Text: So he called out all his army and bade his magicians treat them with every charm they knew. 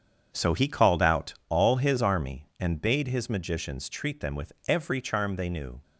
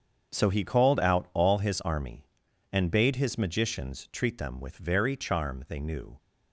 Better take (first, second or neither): first